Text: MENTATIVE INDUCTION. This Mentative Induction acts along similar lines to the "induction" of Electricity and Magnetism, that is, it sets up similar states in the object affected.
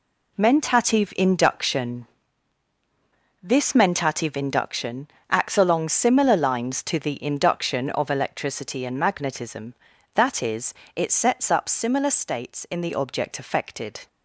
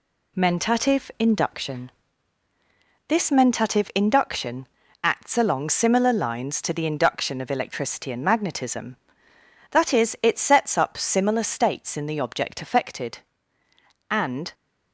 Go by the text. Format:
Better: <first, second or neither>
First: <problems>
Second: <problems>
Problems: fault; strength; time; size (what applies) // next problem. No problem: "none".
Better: first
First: pauses between "Induction" and "acts"; slight; at 5.0 s; 0.22 s long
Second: pauses between "Induction" and "acts"; at 4.6 s; 0.38 s long // goes on to say "And"; slight; from 14.0 s on; 0.44 s long